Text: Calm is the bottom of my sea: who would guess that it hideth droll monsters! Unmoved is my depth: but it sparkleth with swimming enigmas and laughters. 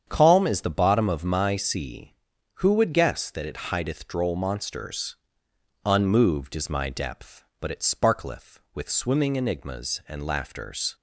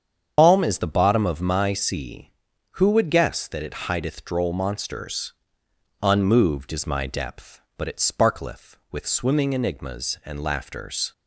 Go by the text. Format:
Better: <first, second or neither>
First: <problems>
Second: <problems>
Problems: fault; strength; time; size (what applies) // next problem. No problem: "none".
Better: first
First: starts louder than the rest; strong; until 1.0 s; 8 dB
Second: loses the start of "Calm"; at 0.3 s; 120 ms // starts louder than the rest; strong; until 1.3 s; 7.5 dB